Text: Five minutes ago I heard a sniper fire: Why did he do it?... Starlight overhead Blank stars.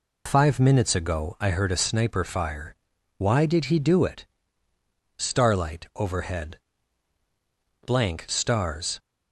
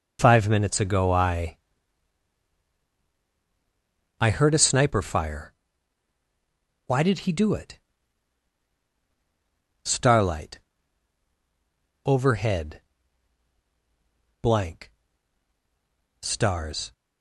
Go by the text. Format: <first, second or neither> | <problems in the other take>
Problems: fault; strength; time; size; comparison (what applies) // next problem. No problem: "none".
first | says "I" twice; at 4.2 s // pauses between "Starlight" and "overhead"; strong; at 10.5 s; 1.4 s long // pauses between "overhead" and "Blank"; strong; at 12.8 s; 1.6 s long; strong in the first // pauses between "Blank" and "stars"; strong; at 14.9 s; 1.3 s long